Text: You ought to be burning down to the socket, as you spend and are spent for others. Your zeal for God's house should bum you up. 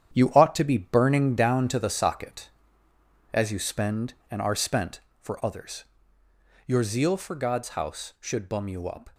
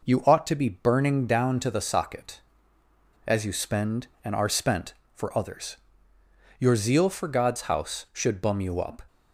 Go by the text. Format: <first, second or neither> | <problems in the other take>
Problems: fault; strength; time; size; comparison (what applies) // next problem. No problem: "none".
second | gets quieter; strong; throughout; 8.5 dB